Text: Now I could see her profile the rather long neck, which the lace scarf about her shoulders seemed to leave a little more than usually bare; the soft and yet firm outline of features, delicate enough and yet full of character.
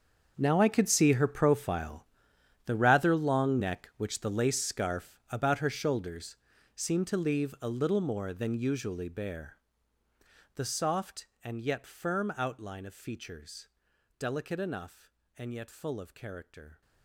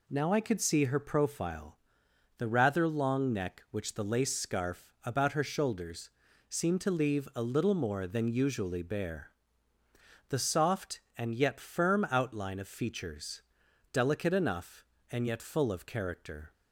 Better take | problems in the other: second | gets quieter; strong; throughout; 17 dB // pauses between "profile" and "the"; noticeable; at 2.0 s; 0.64 s long; noticeable in the second // pauses between "shoulders" and "seemed"; at 6.3 s; 0.40 s long; also in the second

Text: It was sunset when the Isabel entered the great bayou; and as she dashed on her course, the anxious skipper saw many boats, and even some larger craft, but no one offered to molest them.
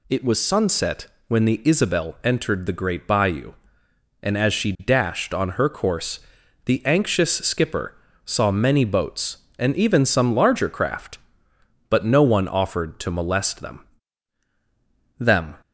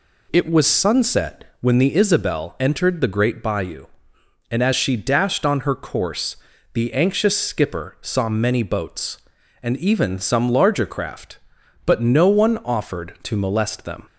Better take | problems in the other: second | pauses between "sunset" and "when"; slight; at 1.0 s; 0.20 s long; slight in the second // pauses between "skipper" and "saw"; slight; at 7.9 s; 0.32 s long // says "them" twice; at 15.1 s

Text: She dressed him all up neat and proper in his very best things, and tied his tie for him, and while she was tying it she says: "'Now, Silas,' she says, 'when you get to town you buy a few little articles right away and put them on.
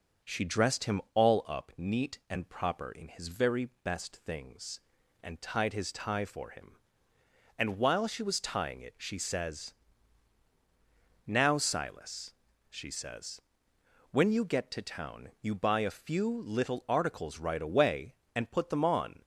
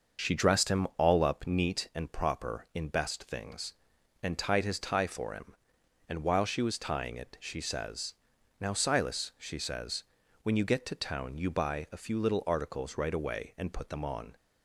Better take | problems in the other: first | starts louder than the rest; until 1.3 s; 6 dB // skips "his very"; at 2.8 s

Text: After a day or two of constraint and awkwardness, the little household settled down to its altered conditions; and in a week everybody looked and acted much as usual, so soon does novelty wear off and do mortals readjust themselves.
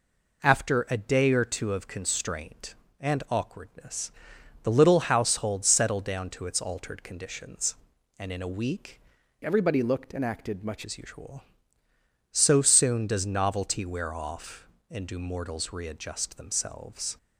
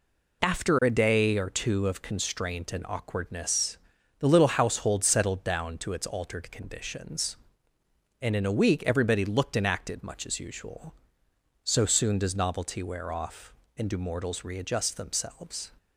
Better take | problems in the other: second | changes voice from "everybody" to "much"; from 9.4 to 10.8 s; 1.4 s long

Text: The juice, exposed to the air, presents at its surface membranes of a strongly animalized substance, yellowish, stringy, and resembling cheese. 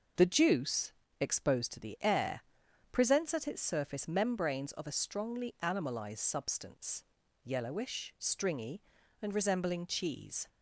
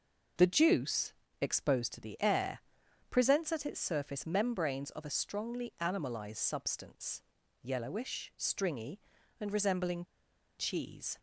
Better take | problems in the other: first | pauses between "resembling" and "cheese"; noticeable; at 10.0 s; 0.53 s long

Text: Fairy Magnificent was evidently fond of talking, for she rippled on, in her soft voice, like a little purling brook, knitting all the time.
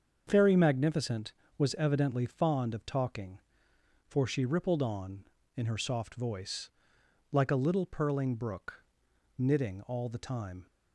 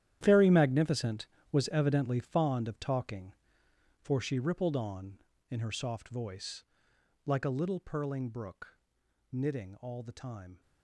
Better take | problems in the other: first | gets quieter; strong; throughout; 14.5 dB // starts louder than the rest; strong; until 1.2 s; 11 dB; also in the first

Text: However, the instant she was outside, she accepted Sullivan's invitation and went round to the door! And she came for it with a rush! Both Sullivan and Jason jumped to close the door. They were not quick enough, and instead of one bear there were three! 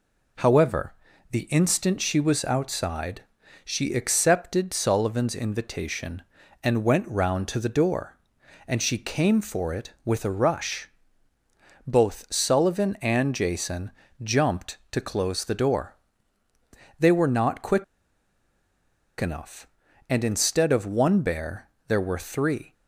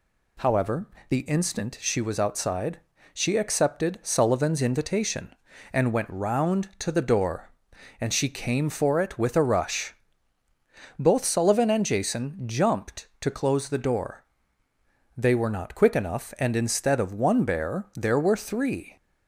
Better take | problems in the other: second | pauses between "Jason" and "jumped"; slight; at 13.9 s; 0.32 s long // pauses between "quick" and "enough"; strong; at 17.8 s; 1.3 s long // pauses between "bear" and "there"; slight; at 21.6 s; 0.22 s long

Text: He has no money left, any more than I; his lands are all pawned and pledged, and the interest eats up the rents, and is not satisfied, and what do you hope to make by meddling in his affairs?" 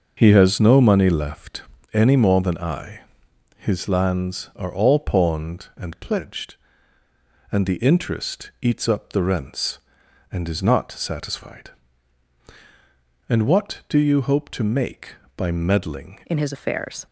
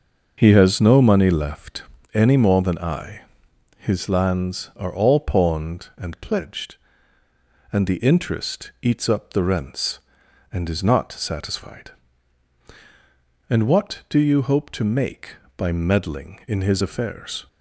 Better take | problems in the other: second | starts louder than the rest; noticeable; until 1.1 s; 6 dB; noticeable in the second // changes voice at "in"; from 16.2 s on; 0.8 s long

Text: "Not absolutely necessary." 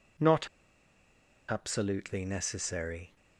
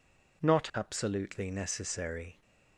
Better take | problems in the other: second | pauses between "Not" and "absolutely"; at 0.4 s; 1.0 s long

